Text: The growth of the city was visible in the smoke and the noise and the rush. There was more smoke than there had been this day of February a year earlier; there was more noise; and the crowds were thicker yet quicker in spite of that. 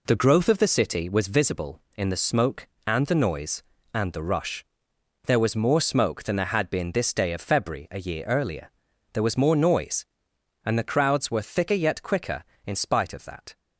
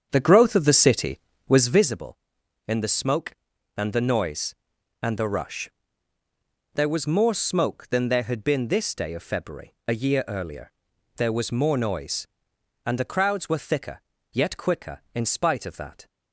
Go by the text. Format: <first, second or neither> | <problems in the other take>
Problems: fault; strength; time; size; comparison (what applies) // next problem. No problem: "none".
first | starts louder than the rest; strong; until 2.0 s; 8 dB // pauses between "thicker" and "yet"; slight; at 13.9 s; 0.32 s long